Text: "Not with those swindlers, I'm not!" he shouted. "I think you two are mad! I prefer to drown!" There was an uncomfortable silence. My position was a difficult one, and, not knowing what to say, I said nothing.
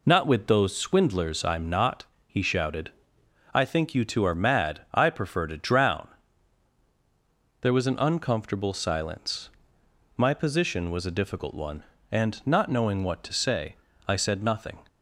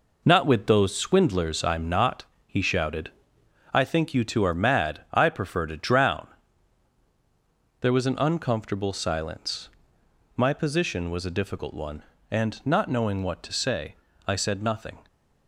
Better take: first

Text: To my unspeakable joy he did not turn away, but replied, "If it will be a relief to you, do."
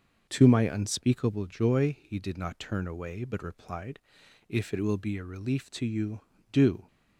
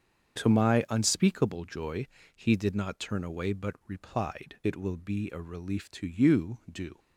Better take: first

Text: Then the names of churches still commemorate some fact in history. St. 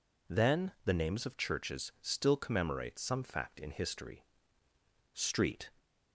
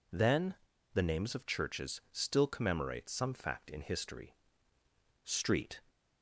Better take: first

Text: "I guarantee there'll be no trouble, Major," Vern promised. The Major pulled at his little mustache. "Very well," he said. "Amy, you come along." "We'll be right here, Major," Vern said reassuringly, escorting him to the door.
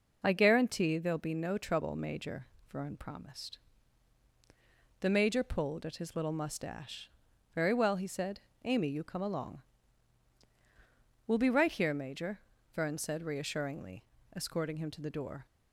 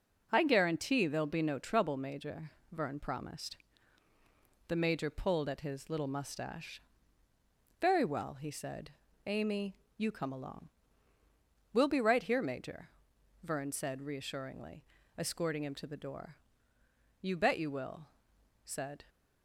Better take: first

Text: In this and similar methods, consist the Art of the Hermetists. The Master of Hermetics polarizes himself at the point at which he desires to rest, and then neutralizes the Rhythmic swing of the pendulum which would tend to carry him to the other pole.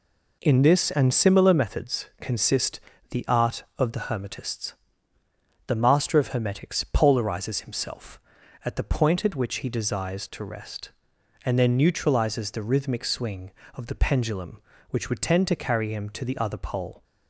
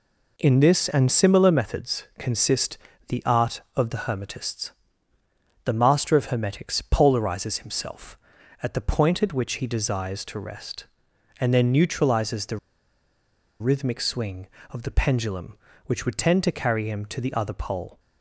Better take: first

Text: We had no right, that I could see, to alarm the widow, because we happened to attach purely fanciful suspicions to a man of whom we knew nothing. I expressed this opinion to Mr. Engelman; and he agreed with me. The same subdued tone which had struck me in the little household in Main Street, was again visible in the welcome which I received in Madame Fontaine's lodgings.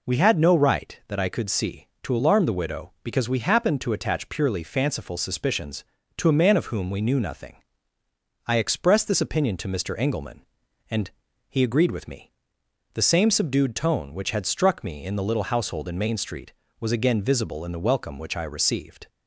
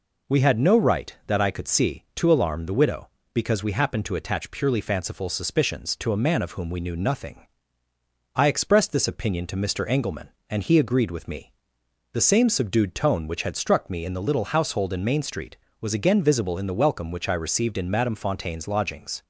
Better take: second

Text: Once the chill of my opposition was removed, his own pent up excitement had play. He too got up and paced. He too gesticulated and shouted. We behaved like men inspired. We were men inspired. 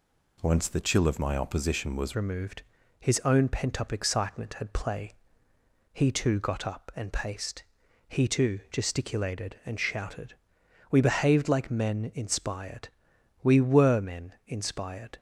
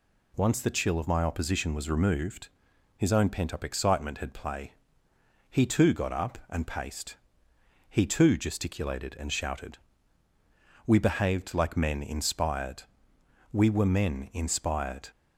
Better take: second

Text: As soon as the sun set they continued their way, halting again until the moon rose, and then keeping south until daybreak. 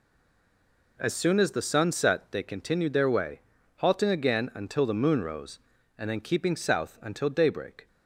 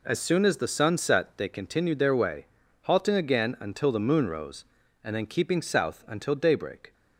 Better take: second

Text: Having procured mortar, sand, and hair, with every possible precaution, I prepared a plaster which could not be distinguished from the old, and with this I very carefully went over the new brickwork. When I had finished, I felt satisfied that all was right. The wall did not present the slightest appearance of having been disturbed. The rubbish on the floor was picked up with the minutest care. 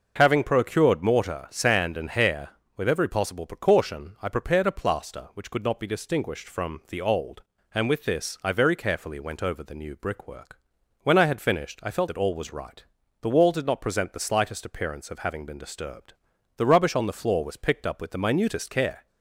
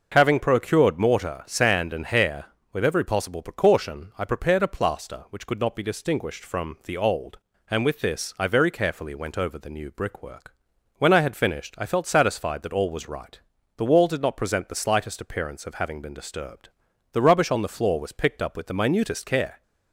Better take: second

